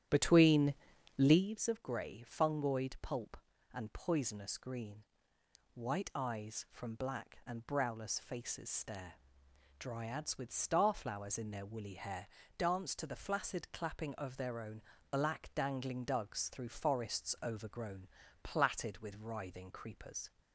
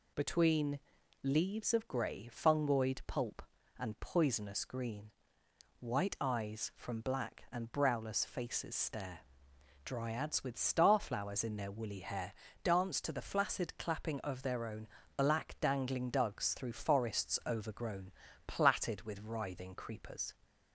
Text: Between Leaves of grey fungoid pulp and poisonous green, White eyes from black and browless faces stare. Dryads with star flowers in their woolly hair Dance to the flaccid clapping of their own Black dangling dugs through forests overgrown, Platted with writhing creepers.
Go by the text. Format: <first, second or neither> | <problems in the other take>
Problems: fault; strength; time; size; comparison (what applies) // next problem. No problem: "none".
second | starts louder than the rest; strong; until 1.5 s; 11 dB // pauses between "Between" and "Leaves"; at 0.7 s; 0.42 s long; also in the second // pauses between "hair" and "Dance"; slight; at 12.2 s; 0.32 s long; slight in the second // pauses between "own" and "Black"; slight; at 14.8 s; 0.28 s long; slight in the second